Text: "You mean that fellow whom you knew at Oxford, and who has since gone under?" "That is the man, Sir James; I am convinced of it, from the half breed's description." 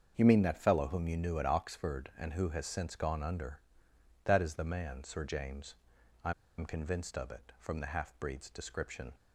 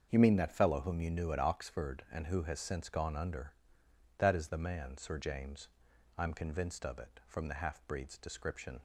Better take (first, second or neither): second